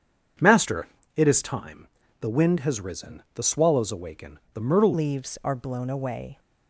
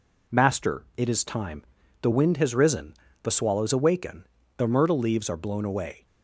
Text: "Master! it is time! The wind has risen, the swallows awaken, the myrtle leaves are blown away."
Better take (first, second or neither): second